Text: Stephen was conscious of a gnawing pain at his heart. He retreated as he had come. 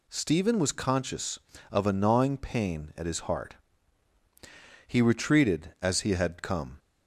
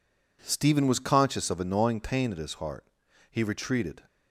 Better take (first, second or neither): first